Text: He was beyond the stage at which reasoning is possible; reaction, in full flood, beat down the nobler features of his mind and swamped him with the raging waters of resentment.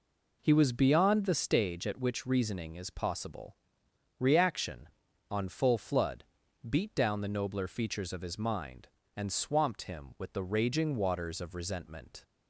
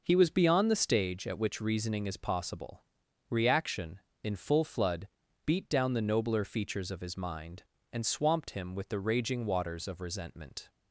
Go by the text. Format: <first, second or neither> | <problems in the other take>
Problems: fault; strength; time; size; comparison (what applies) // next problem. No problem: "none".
second | says "on" for "in"; at 5.2 s